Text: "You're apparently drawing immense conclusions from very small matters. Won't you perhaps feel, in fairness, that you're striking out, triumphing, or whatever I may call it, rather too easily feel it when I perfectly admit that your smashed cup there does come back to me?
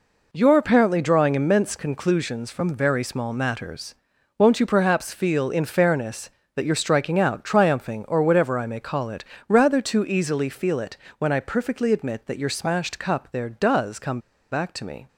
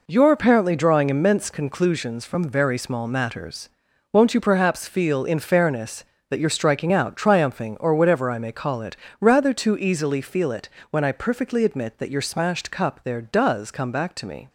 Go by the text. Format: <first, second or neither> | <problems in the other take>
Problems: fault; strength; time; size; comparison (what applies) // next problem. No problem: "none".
second | pauses between "it" and "when"; slight; at 10.9 s; 0.22 s long; slight in the second // pauses between "come" and "back"; slight; at 14.1 s; 0.32 s long